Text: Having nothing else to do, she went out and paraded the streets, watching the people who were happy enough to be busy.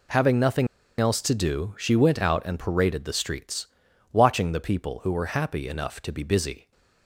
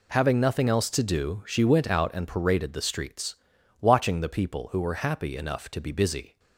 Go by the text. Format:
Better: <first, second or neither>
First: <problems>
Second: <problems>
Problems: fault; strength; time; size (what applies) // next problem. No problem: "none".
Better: second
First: pauses between "nothing" and "else"; slight; at 0.6 s; 0.32 s long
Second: none